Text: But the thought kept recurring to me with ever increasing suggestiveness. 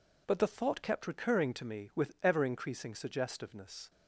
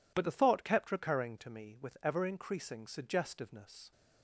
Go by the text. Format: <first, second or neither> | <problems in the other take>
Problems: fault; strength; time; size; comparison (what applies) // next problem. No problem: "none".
neither | none